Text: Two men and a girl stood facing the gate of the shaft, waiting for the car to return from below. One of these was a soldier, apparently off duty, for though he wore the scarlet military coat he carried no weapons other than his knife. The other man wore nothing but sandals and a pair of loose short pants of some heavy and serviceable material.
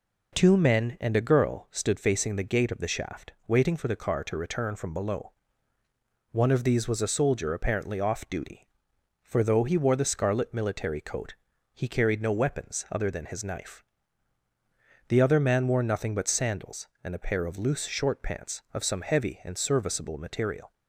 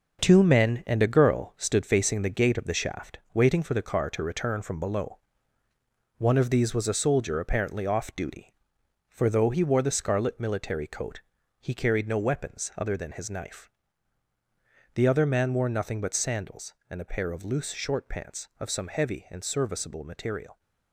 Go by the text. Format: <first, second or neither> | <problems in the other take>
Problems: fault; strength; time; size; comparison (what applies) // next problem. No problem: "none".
first | gets quieter; strong; throughout; 7.5 dB // pauses between "coat" and "he"; at 11.2 s; 0.40 s long; also in the first